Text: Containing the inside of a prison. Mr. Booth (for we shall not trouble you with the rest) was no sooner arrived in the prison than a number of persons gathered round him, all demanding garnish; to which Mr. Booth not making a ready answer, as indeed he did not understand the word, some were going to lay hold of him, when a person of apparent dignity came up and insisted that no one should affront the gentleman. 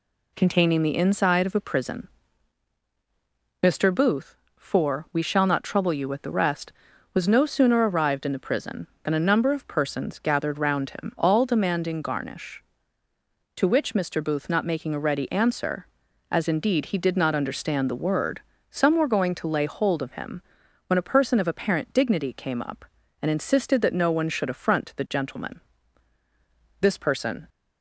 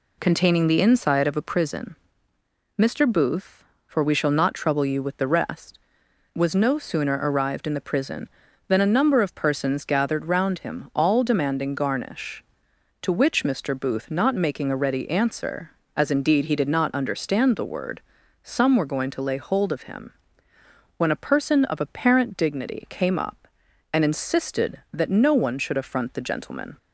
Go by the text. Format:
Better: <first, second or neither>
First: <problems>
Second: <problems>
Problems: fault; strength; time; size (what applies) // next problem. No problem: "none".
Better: second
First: goes on to say "This person"; noticeable; from 26.8 s on; 0.68 s long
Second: none